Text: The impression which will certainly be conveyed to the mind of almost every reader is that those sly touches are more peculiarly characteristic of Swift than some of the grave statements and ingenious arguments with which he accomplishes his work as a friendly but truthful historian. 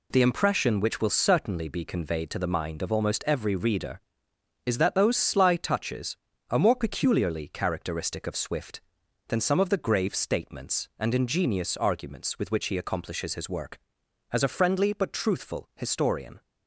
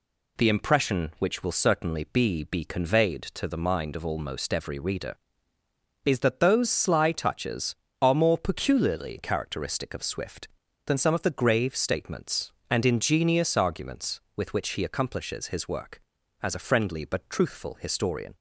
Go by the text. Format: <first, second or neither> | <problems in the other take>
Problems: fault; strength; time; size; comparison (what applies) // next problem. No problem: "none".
first | says "be" twice; at 2.4 s